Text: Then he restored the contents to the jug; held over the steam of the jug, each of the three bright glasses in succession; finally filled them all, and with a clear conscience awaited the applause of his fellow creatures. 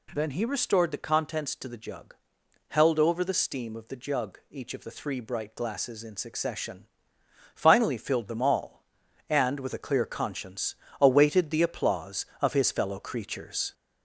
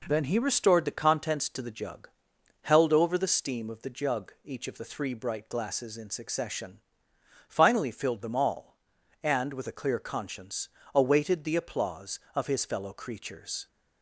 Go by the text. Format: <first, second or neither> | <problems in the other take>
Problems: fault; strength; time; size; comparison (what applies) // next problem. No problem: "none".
second | gets louder; slight; throughout; 3 dB // pauses between "conscience" and "awaited"; slight; at 10.7 s; 0.26 s long; slight in the second